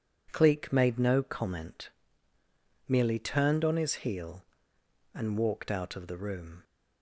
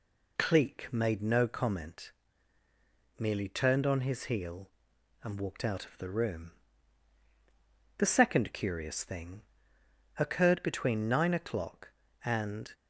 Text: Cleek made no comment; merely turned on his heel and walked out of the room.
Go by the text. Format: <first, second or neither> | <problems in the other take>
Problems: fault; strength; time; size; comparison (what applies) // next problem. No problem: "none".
first | goes on to say "The second curious thing occurred between nine o'clock and"; strong; from 7.9 s on; 4.7 s long